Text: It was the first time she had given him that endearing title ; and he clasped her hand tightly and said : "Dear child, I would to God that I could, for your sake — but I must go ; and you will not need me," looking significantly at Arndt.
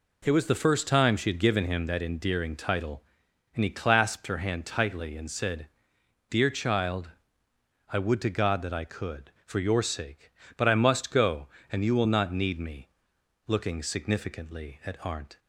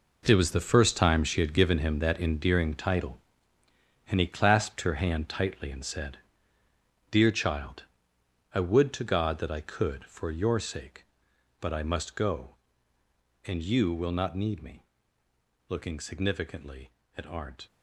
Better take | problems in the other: first | gets quieter; strong; throughout; 12.5 dB

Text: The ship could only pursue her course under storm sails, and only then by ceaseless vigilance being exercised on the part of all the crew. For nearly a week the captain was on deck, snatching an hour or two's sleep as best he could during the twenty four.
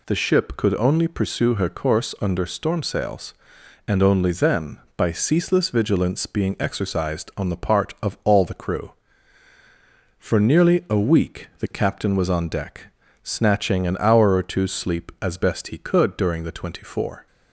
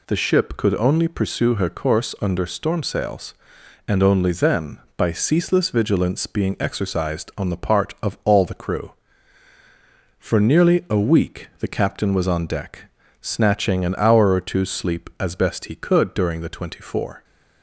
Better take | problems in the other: neither | none

